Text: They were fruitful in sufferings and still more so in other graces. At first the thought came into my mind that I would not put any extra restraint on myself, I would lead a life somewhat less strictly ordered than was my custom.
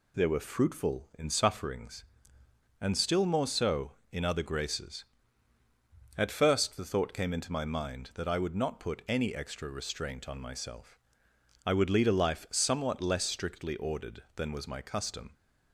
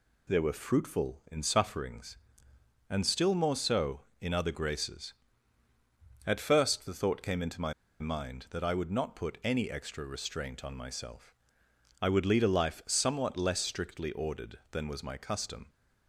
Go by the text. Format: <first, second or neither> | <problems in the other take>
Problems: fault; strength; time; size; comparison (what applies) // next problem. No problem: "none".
first | pauses between "my" and "mind"; slight; at 7.7 s; 0.28 s long